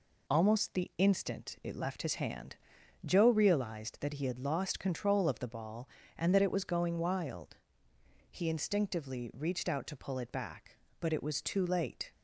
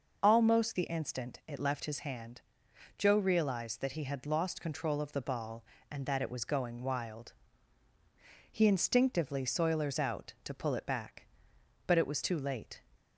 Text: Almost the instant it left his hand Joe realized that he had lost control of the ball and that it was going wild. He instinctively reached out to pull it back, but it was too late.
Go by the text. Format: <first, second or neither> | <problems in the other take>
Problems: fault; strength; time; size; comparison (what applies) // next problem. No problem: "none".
first | pauses between "hand" and "Joe"; noticeable; at 2.4 s; 0.56 s long; noticeable in the first // says "soilers" for "reached"; at 9.4 s